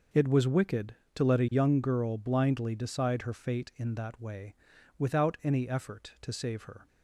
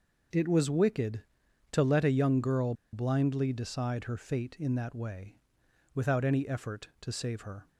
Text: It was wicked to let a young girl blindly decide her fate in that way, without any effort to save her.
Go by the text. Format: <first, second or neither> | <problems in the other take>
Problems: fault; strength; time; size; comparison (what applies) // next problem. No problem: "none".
first | starts louder than the rest; until 1.8 s; 6.5 dB // pauses between "girl" and "blindly"; slight; at 2.7 s; 0.20 s long